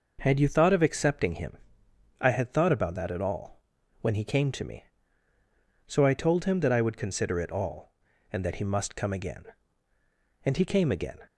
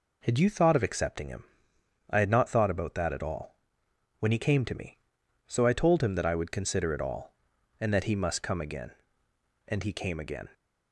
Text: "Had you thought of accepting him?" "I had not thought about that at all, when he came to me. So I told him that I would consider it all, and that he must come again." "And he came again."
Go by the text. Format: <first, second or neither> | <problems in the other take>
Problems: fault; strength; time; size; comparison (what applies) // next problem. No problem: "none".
second | skips "not"; at 2.5 s